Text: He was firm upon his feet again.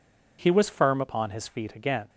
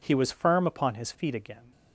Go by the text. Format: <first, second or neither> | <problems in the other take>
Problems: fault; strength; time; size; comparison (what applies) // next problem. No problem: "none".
neither | none